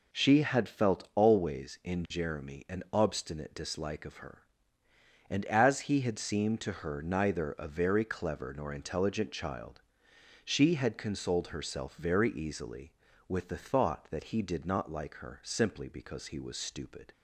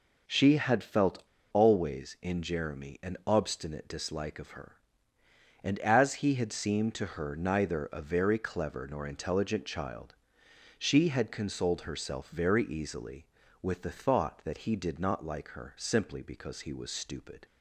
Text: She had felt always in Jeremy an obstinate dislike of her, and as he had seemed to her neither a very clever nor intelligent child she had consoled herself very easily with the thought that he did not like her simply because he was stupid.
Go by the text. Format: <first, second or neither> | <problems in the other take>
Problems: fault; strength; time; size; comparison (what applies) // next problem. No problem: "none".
first | pauses between "felt" and "always"; slight; at 1.2 s; 0.29 s long // pauses between "child" and "she"; noticeable; at 10.1 s; 0.64 s long; noticeable in the first